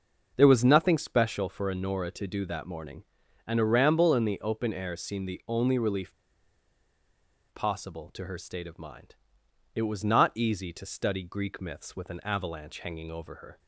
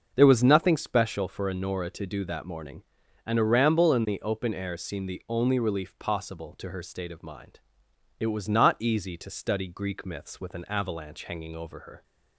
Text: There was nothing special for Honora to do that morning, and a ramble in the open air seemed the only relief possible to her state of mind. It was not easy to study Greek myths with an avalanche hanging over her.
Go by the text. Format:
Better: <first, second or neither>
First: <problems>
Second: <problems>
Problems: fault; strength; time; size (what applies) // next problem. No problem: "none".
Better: second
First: starts louder than the rest; noticeable; until 1.3 s; 6 dB // pauses between "relief" and "possible"; strong; at 6.1 s; 1.3 s long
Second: starts louder than the rest; until 1.1 s; 6.5 dB